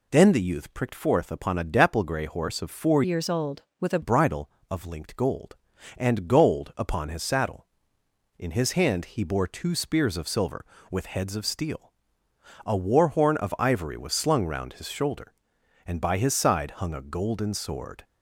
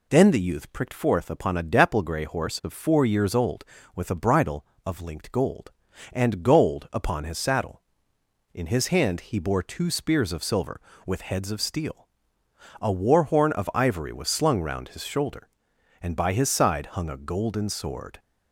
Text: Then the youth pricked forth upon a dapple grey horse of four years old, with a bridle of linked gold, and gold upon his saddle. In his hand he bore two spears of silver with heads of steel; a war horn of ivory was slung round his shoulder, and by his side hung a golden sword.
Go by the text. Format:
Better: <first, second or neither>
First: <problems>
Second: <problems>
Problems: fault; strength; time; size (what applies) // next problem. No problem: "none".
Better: second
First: changes voice from "years" to "a"; from 3.0 to 4.0 s; 1.0 s long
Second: none